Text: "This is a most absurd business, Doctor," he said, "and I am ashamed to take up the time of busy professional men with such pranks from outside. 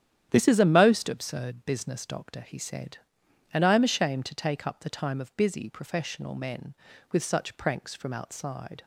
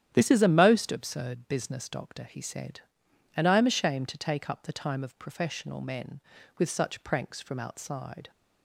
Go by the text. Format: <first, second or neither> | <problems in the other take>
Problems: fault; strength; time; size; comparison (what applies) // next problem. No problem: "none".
first | starts louder than the rest; strong; until 1.1 s; 10 dB; strong in the first // skips "busy"; at 5.1 s